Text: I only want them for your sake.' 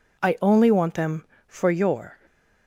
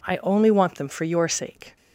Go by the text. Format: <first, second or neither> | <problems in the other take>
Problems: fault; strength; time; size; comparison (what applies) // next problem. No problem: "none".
second | stops before "sake"; at 2.2 s